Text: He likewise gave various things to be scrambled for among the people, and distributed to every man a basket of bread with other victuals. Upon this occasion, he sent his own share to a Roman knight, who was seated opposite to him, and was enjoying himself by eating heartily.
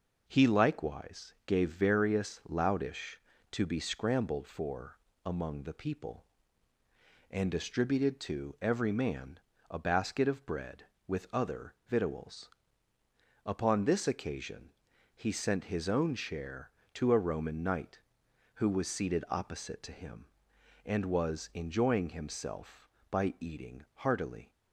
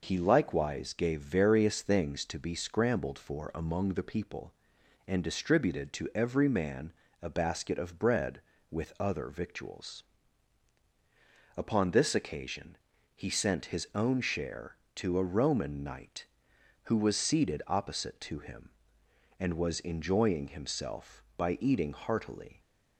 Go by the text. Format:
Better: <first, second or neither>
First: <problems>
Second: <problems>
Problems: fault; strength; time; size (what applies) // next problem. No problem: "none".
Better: second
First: says "loudish" for "things"; at 2.4 s // pauses between "for" and "among"; slight; at 4.9 s; 0.26 s long // pauses between "man" and "a"; slight; at 9.3 s; 0.30 s long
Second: pauses between "man" and "a"; slight; at 6.9 s; 0.30 s long